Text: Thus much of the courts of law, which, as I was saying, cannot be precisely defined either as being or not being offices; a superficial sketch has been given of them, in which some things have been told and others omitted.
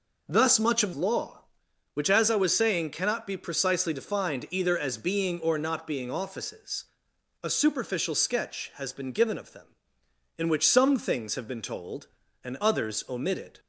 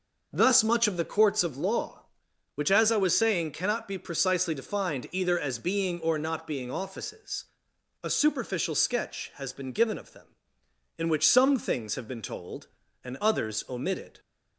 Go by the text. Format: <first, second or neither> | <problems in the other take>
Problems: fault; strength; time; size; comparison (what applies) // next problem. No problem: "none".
second | skips "the courts of"; at 0.9 s